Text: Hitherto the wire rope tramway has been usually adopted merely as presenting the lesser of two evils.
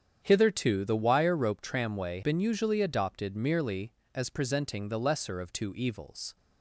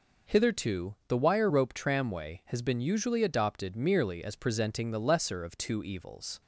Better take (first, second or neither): second